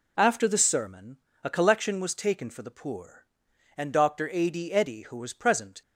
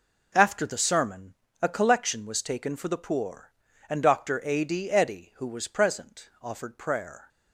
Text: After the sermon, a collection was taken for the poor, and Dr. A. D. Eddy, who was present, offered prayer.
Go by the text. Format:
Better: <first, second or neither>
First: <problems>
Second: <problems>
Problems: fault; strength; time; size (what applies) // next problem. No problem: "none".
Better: second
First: stops before "offered prayer"; at 5.8 s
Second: none